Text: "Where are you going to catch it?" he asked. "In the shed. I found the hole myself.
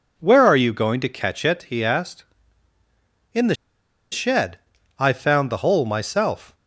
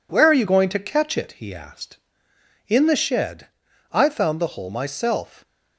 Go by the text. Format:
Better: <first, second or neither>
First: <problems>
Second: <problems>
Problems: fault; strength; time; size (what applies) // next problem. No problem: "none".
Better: second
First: pauses between "the" and "shed"; noticeable; at 3.5 s; 0.57 s long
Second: none